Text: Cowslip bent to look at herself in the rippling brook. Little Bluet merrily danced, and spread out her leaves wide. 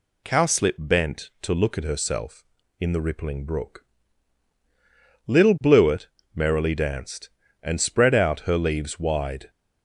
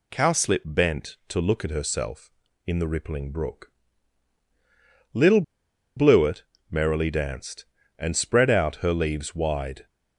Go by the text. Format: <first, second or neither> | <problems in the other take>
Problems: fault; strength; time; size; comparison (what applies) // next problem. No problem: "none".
first | pauses between "Little" and "Bluet"; noticeable; at 5.4 s; 0.54 s long // pauses between "Bluet" and "merrily"; slight; at 6.4 s; 0.28 s long; slight in the first